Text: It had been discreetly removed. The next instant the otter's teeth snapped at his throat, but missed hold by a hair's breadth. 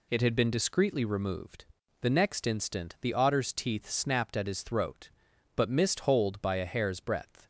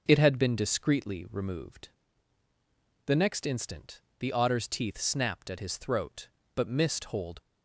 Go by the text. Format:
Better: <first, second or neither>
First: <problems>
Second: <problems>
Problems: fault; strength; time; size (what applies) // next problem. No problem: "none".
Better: first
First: none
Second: starts louder than the rest; until 1.0 s; 6.5 dB // pauses between "instant" and "the"; slight; at 4.0 s; 0.18 s long // stops before "by a hair's breadth"; at 7.4 s